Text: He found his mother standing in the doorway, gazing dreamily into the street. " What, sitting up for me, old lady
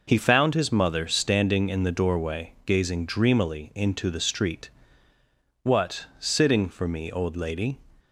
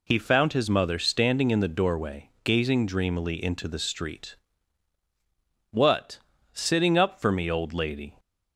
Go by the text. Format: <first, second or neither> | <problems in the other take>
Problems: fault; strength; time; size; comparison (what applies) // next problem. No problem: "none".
second | skips "up"; at 6.6 s